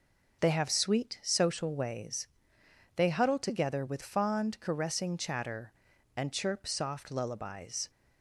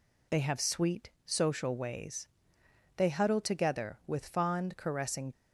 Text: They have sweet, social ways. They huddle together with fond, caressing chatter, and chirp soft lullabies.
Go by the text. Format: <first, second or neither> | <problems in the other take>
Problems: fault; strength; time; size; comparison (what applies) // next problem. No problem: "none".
first | stops before "chatter and chirp soft lullabies"; at 5.3 s